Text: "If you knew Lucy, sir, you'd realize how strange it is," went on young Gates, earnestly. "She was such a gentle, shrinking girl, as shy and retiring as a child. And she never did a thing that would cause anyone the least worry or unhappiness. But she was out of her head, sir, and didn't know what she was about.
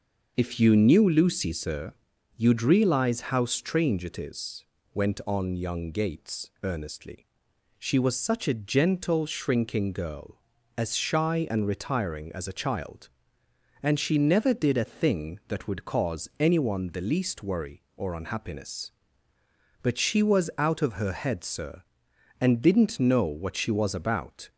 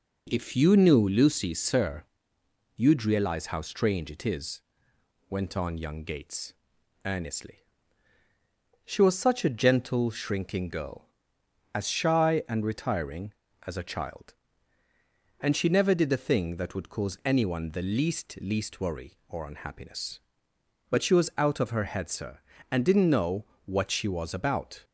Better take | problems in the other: first | says "least" twice; at 18.4 s // pauses between "know" and "what"; slight; at 23.4 s; 0.18 s long

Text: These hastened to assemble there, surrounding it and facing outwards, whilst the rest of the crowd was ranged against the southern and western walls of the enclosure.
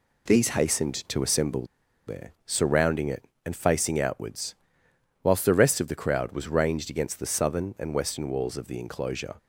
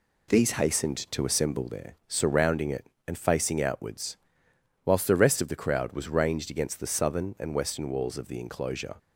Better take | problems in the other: second | pauses between "assemble" and "there"; at 1.6 s; 0.42 s long

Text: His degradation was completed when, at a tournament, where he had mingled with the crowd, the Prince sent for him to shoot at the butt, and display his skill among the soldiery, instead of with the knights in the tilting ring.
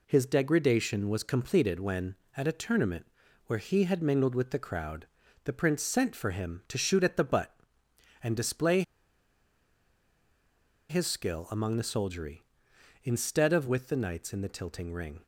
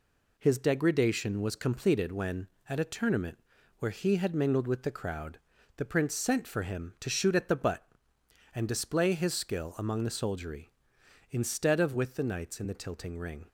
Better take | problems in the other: second | pauses between "display" and "his"; strong; at 8.8 s; 2.0 s long

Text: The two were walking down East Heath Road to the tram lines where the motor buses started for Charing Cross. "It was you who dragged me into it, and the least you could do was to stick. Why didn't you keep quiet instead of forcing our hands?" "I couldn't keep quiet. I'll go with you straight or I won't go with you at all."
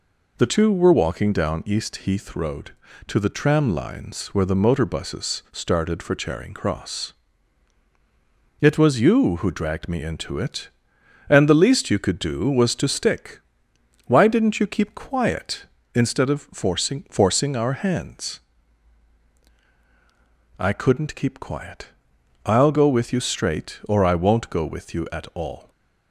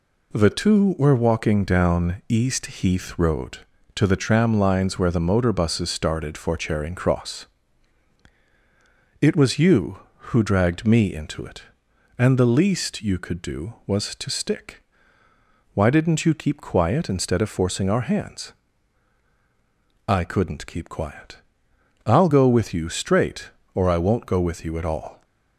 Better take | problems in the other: second | says "forcing" twice; at 17.0 s

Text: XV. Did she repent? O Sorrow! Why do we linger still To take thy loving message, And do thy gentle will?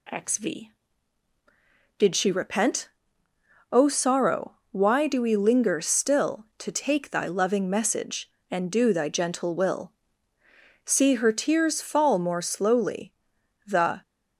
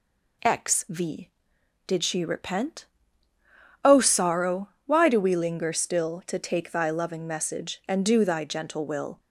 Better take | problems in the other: second | goes on to say "See her tears fall more slowly The"; strong; from 10.8 s on; 3.1 s long

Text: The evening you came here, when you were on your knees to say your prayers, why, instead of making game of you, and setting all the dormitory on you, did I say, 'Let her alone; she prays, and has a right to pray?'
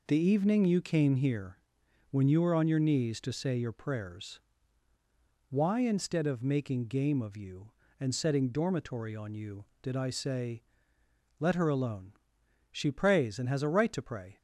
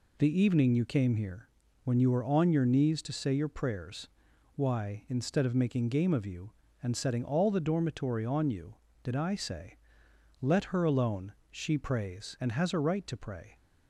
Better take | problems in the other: second | skips "all the"; at 8.5 s

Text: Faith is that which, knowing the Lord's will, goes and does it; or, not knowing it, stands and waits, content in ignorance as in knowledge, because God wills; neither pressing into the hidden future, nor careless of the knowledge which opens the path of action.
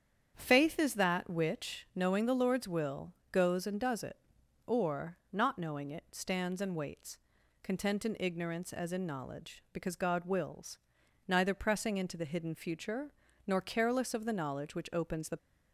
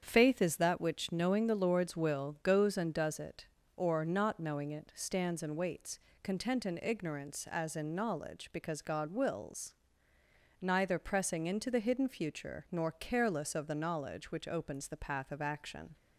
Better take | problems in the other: second | starts louder than the rest; strong; until 1.3 s; 8.5 dB; strong in the second // stops before "path of action"; at 15.3 s

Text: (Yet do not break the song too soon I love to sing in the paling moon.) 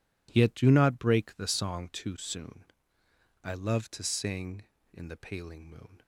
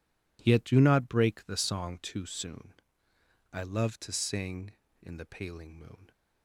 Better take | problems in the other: neither | pauses between "soon" and "I"; noticeable; the same in both

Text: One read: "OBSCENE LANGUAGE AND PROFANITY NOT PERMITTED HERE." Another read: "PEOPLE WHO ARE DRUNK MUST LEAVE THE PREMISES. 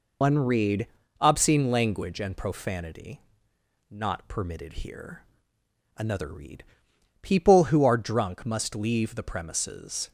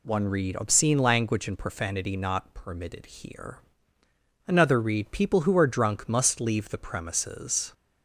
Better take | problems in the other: second | loses the start of "One"; at 0.2 s; 65 ms // pauses between "PROFANITY" and "NOT"; noticeable; at 3.1 s; 0.70 s long

